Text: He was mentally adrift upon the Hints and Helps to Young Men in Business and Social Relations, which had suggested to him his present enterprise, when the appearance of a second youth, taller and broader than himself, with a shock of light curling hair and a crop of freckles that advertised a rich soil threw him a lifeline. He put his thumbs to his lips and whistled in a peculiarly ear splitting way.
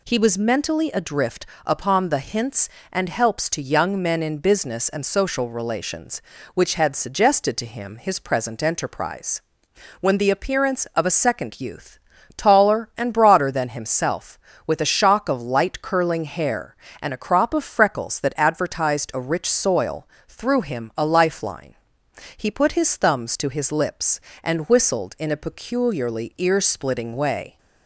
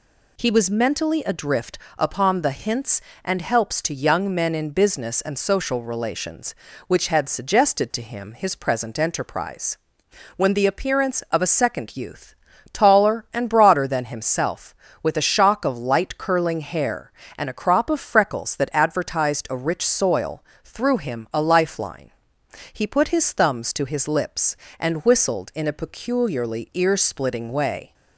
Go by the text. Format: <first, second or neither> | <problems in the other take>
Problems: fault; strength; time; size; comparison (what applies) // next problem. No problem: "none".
neither | pauses between "adrift" and "upon"; slight; the same in both // pauses between "soil" and "threw"; slight; the same in both